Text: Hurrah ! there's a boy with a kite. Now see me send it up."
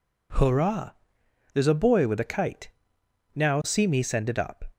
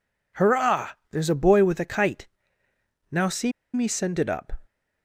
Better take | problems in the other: first | pauses between "see" and "me"; slight; at 3.5 s; 0.22 s long

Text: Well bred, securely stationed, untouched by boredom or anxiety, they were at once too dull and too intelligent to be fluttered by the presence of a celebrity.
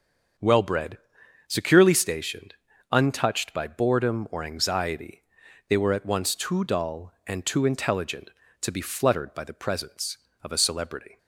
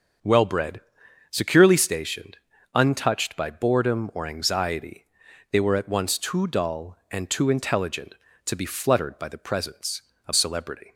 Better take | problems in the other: first | starts louder than the rest; until 1.7 s; 6.5 dB; also in the first // skips "a"; at 10.3 s

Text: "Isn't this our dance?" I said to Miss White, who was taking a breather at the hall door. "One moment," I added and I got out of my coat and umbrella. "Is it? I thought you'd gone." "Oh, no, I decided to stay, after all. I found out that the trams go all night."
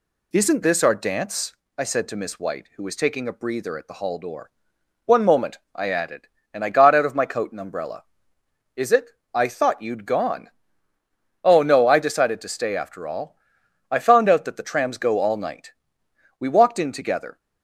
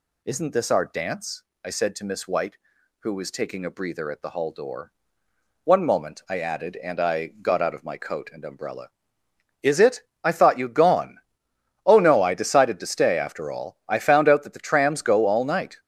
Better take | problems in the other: second | goes on to say "We walked in together"; noticeable; from 16.3 s on; 1.0 s long

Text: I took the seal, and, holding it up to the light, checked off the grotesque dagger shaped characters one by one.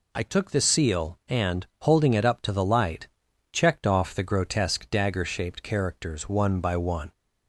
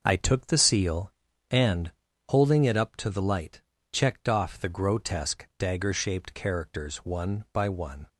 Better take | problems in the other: first | gets quieter; strong; throughout; 7.5 dB

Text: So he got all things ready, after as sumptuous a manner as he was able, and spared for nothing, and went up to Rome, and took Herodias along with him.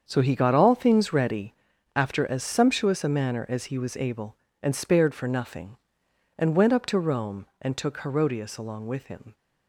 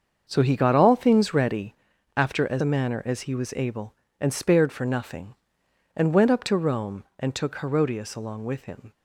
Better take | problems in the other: first | starts louder than the rest; until 1.2 s; 7 dB; strong in the first // skips "sumptuous"; at 2.6 s

